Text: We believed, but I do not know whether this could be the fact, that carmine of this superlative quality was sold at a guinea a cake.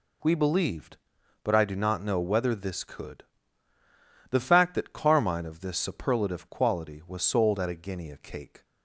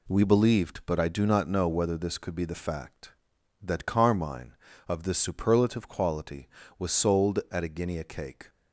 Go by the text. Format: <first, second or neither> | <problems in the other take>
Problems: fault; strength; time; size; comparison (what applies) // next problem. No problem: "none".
second | skips "be"; at 3.7 s